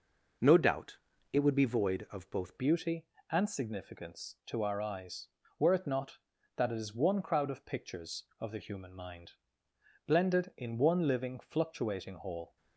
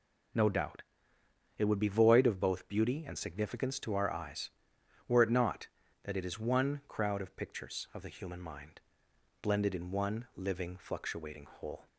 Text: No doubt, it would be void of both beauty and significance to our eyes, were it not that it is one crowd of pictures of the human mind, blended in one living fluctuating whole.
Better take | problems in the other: second | changes voice at "beauty"; from 2.5 s on; 10.0 s long

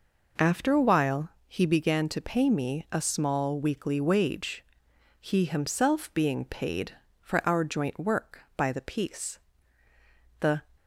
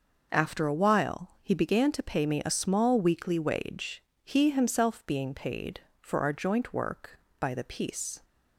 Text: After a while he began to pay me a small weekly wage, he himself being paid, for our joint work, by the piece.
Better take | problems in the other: second | pauses between "while" and "he"; slight; at 1.3 s; 0.18 s long // goes on to say "The"; slight; from 10.3 s on; 0.26 s long

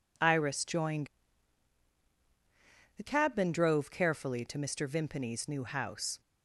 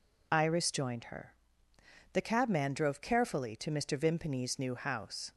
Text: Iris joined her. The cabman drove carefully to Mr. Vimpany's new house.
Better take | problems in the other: second | skips "her"; at 2.0 s

